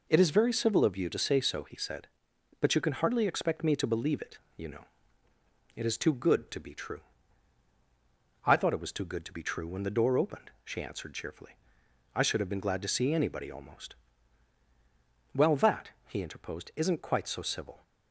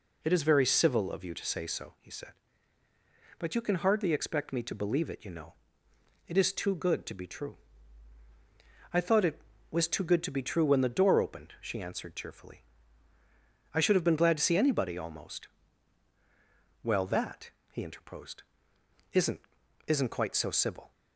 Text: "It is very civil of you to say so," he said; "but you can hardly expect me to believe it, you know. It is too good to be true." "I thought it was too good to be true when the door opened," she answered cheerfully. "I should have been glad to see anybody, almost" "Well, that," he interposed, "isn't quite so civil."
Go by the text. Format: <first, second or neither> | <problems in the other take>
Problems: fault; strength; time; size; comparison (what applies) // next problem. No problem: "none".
first | pauses between "almost" and "Well"; strong; at 15.4 s; 1.3 s long; strong in the first // says "isn't" twice; at 19.8 s